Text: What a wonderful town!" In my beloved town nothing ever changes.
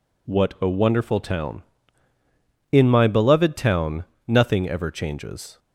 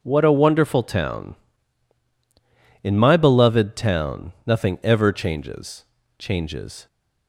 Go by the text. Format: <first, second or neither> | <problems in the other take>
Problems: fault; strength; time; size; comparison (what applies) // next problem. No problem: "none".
first | pauses between "town" and "nothing"; slight; at 4.3 s; 0.16 s long; slight in the first // says "changes" twice; at 6.1 s